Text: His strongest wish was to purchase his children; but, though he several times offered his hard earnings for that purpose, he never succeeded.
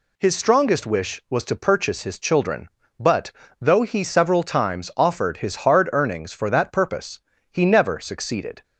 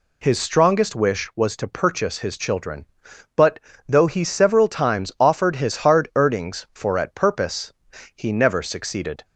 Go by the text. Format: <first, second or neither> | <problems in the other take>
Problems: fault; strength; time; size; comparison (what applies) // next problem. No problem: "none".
first | says "at" for "that"; at 6.9 s